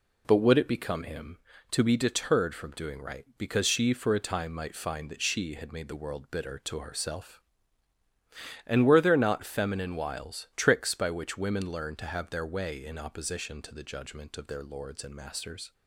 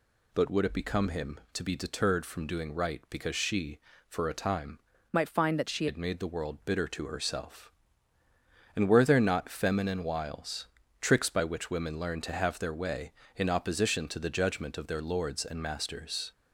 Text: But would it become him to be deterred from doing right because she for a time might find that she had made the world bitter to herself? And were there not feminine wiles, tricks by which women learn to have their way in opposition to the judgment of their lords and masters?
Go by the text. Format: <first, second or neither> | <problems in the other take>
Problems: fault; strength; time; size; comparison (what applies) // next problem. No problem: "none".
first | changes voice from "might" to "she"; from 5.1 to 5.8 s; 0.7 s long